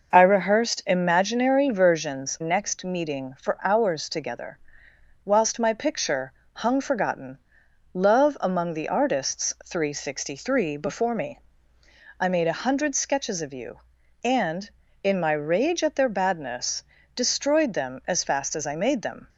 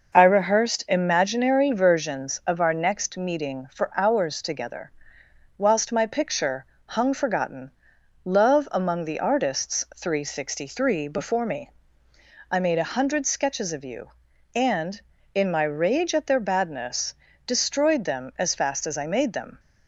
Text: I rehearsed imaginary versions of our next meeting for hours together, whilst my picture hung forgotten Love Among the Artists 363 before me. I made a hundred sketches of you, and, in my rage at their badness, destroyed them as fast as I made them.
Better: second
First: skips "of our"; at 2.3 s // pauses between "picture" and "hung"; slight; at 6.3 s; 0.20 s long // pauses between "forgotten" and "Love"; noticeable; at 7.3 s; 0.56 s long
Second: pauses between "picture" and "hung"; slight; at 6.6 s; 0.20 s long // pauses between "forgotten" and "Love"; noticeable; at 7.7 s; 0.54 s long

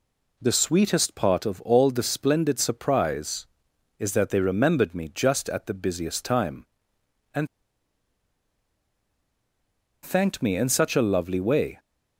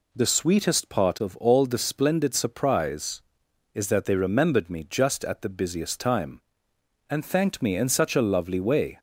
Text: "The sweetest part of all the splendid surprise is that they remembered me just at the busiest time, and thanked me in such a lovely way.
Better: second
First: pauses between "and" and "thanked"; strong; at 7.4 s; 2.5 s long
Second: none

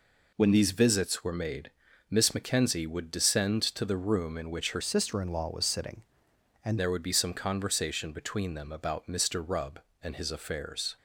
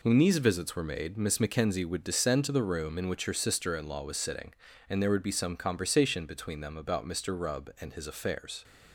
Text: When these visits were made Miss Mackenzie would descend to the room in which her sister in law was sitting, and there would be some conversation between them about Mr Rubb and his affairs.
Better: second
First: pauses between "made" and "Miss"; at 1.6 s; 0.40 s long // changes voice from "sister" to "and"; from 4.8 to 6.7 s; 1.9 s long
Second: none

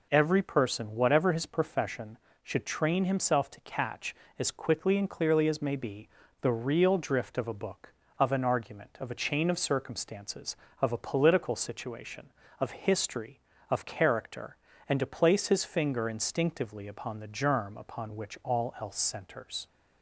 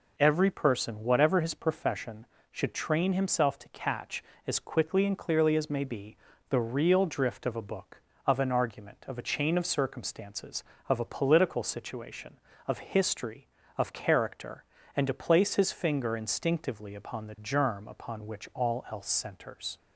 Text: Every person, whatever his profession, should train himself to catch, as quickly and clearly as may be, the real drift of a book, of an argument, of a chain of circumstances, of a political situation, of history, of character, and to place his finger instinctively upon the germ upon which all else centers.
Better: neither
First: none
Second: none

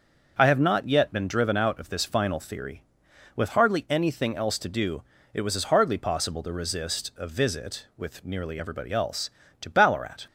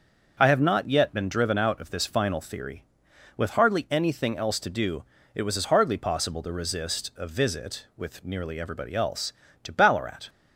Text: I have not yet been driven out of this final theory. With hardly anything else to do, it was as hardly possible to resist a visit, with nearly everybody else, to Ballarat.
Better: neither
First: starts louder than the rest; until 1.3 s; 6.5 dB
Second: starts louder than the rest; until 1.4 s; 6.5 dB

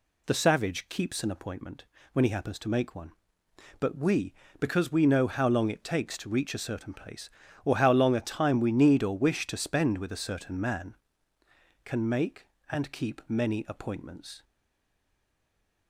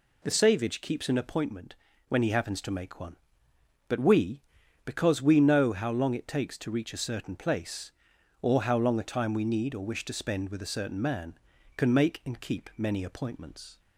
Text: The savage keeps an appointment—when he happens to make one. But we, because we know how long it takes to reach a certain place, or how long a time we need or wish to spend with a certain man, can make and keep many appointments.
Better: second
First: stays silent after the last word; noticeable; from 14.4 s on; 1.4 s long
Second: none

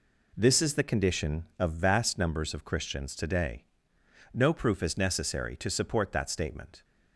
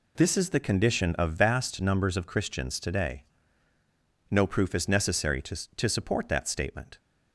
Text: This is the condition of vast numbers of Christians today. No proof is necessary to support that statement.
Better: first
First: none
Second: says "to" twice; at 5.7 s

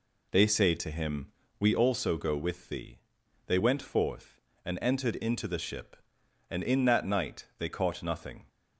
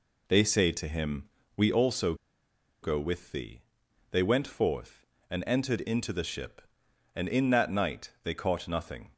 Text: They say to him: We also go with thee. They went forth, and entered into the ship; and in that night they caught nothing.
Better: first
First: none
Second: pauses between "also" and "go"; noticeable; at 2.1 s; 0.68 s long

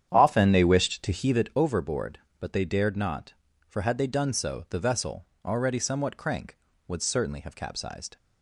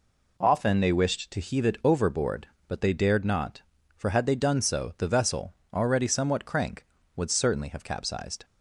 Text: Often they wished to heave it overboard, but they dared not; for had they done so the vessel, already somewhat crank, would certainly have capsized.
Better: second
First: starts louder than the rest; strong; until 1.5 s; 9 dB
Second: none

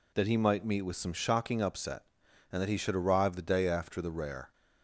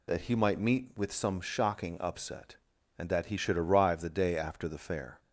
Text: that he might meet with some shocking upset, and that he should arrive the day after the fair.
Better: second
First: says "rare" for "fair"; at 4.1 s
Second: none

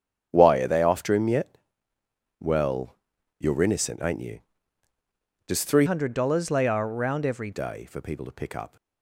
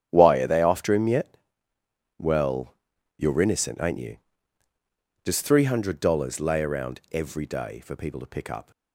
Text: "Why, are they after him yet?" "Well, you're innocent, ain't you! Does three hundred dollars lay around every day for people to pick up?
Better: second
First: starts louder than the rest; strong; until 1.3 s; 8 dB // changes voice from "hundred" to "every"; from 5.8 to 7.5 s; 1.7 s long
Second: starts louder than the rest; strong; until 1.1 s; 9 dB

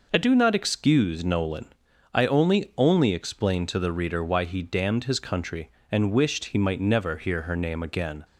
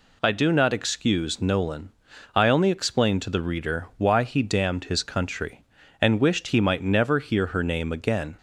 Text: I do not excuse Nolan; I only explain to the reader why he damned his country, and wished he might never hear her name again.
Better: second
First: says "only" twice; at 2.7 s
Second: none

